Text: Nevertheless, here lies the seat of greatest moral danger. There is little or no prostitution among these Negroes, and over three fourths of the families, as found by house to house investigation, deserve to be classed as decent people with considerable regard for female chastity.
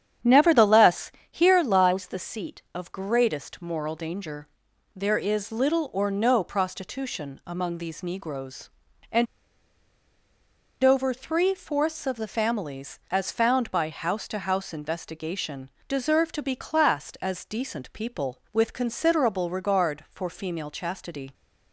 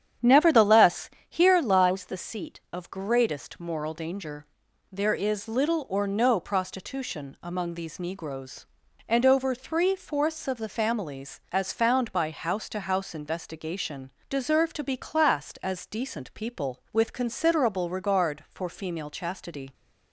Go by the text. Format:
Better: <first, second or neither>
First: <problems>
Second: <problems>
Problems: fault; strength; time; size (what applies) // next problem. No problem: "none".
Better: second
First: starts louder than the rest; strong; until 1.4 s; 9 dB // pauses between "and" and "over"; strong; at 9.2 s; 1.5 s long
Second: starts louder than the rest; strong; until 1.4 s; 9 dB